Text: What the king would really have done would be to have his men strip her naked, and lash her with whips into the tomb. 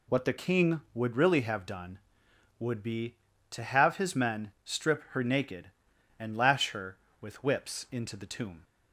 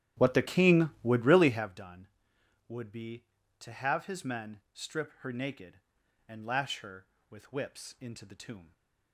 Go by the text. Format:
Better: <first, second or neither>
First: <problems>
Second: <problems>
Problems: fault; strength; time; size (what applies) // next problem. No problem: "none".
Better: first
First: none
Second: starts louder than the rest; strong; until 1.8 s; 11.5 dB